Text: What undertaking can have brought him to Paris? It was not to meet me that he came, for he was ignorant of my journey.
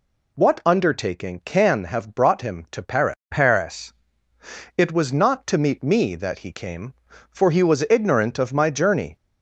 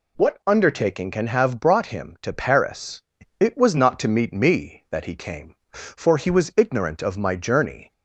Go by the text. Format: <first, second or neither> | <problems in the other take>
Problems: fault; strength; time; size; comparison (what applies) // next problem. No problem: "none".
second | says "Paris" twice; at 3.2 s